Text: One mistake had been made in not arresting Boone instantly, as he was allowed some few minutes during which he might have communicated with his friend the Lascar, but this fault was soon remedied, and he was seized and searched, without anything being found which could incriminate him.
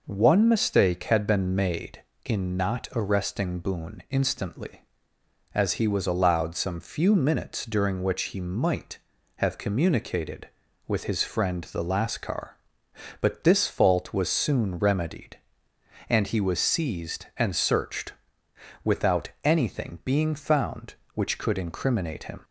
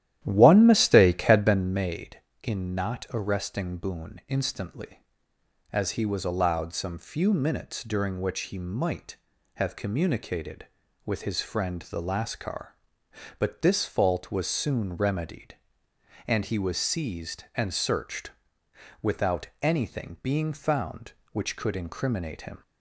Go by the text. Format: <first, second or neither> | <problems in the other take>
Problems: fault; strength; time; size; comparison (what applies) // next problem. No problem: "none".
first | starts louder than the rest; strong; until 1.7 s; 12 dB